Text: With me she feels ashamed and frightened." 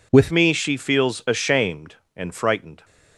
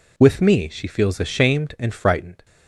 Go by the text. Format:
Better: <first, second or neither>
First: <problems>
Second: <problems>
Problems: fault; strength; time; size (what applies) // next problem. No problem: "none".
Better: second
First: changes voice at "me"; from 0.3 s on; 2.5 s long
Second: none